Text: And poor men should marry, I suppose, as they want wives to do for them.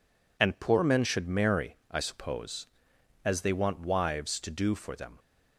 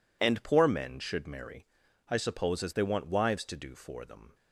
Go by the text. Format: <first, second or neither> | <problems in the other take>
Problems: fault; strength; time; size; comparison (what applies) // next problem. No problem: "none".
neither | none